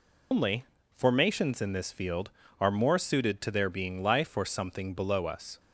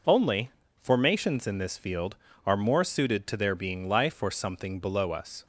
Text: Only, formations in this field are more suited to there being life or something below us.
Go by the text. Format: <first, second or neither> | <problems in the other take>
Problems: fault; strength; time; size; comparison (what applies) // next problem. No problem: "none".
second | loses the start of "Only"; at 0.3 s; 115 ms